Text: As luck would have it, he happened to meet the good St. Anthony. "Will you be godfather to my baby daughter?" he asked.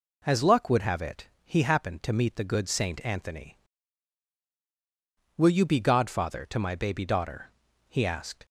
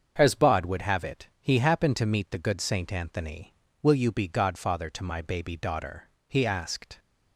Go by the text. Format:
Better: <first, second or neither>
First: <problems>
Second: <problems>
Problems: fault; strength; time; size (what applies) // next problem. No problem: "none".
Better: first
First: none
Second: starts louder than the rest; until 1.1 s; 7 dB // says "bod" for "luck"; at 0.3 s